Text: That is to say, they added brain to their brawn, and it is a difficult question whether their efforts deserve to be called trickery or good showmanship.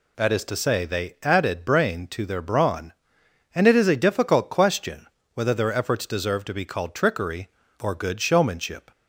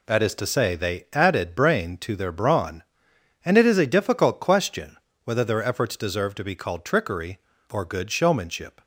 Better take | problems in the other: first | gets quieter; strong; throughout; 7.5 dB // pauses between "question" and "whether"; slight; at 4.9 s; 0.26 s long; slight in the first

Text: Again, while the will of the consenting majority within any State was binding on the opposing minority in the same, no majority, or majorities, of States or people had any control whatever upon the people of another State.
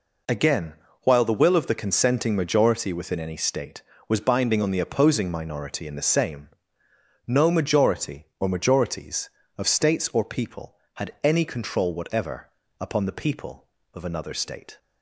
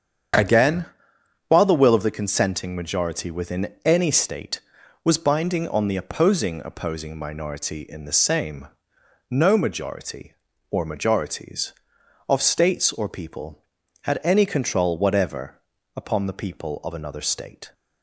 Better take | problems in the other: first | starts louder than the rest; strong; until 1.9 s; 8 dB // says "opposing" twice; at 6.6 s // pauses between "whatever" and "upon"; slight; at 15.6 s; 0.34 s long; slight in the first

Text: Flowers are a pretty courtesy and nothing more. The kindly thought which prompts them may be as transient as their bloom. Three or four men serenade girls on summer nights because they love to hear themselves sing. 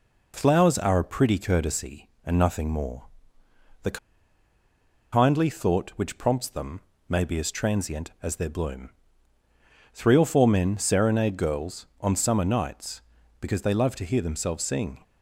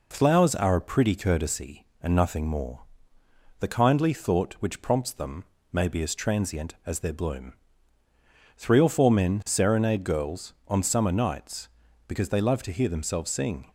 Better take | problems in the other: second | pauses between "The" and "kindly"; at 3.9 s; 1.1 s long // pauses between "them" and "may"; slight; at 6.8 s; 0.26 s long; slight in the second

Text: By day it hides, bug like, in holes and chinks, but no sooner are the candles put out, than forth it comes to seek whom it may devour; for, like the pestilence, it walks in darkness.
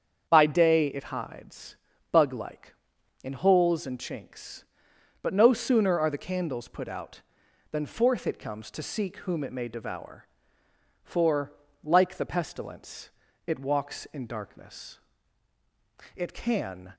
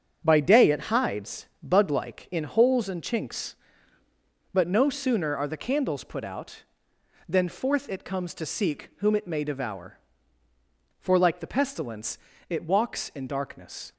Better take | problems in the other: second | starts louder than the rest; strong; until 1.3 s; 7.5 dB; strong in the second // goes on to say "It can"; noticeable; from 16.1 s on; 0.78 s long

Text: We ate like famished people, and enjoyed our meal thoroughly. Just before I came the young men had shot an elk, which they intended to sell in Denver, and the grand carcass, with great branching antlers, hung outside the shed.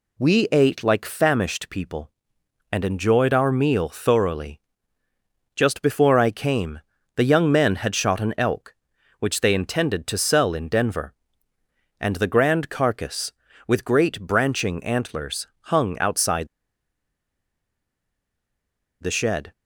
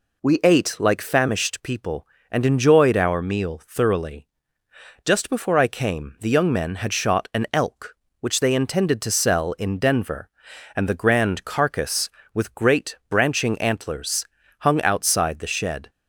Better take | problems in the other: second | pauses between "came" and "the"; at 6.7 s; 0.38 s long // pauses between "outside" and "the"; strong; at 16.4 s; 2.5 s long

